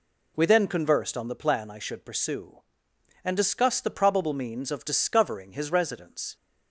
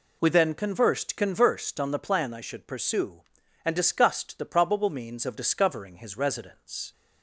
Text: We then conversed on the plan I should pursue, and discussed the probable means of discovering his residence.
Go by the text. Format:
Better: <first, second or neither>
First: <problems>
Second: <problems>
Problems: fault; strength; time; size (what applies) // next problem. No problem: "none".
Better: first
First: none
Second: says "conversed" twice; at 1.1 s